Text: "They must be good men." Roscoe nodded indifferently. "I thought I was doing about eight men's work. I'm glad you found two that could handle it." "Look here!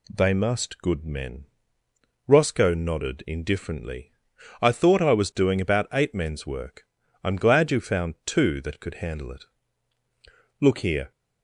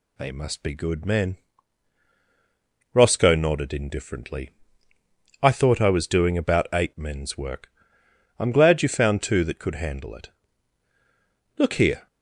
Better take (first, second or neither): second